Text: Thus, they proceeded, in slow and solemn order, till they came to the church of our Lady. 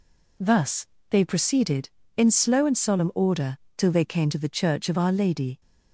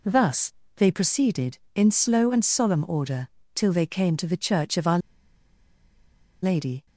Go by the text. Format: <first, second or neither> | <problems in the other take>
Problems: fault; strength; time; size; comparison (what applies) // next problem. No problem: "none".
first | pauses between "our" and "Lady"; strong; at 4.9 s; 1.4 s long